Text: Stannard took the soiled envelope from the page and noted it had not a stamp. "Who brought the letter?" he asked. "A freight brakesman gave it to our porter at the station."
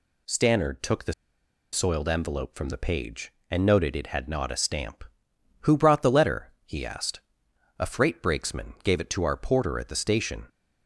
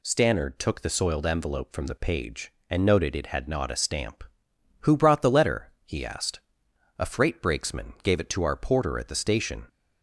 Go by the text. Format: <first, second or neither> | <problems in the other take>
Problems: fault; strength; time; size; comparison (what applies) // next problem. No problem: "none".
second | pauses between "the" and "soiled"; noticeable; at 1.1 s; 0.59 s long